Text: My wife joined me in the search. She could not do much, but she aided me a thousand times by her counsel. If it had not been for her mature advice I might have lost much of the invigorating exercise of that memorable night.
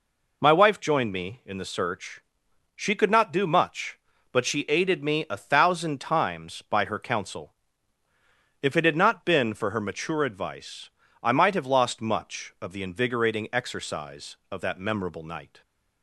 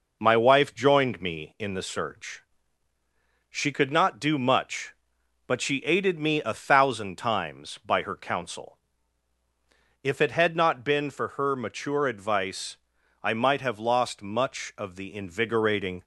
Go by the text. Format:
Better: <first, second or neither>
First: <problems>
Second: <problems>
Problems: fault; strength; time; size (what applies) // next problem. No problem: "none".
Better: first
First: pauses between "advice" and "I"; slight; at 10.8 s; 0.34 s long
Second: pauses between "advice" and "I"; noticeable; at 12.7 s; 0.46 s long // stops before "exercise of that memorable night"; at 16.0 s